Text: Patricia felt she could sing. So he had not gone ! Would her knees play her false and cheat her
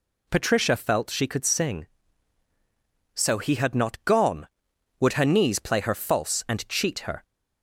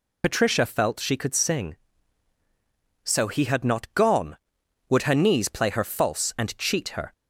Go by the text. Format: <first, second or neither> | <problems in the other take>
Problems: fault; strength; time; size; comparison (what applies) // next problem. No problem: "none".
first | loses the start of "Patricia"; at 0.2 s; 55 ms